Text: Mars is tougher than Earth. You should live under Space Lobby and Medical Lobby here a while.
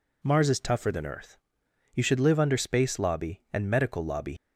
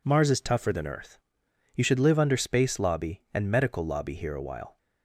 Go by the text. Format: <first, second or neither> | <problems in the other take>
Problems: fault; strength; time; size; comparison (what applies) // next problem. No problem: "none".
second | stops before "here a while"; at 4.3 s